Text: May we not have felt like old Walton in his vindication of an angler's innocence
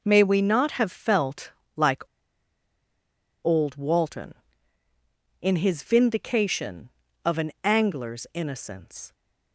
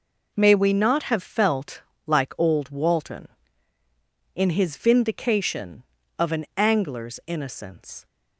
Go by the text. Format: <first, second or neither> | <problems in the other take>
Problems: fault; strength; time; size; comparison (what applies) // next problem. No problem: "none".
second | pauses between "felt" and "like"; slight; at 1.5 s; 0.26 s long; slight in the second // pauses between "like" and "old"; strong; at 2.0 s; 1.4 s long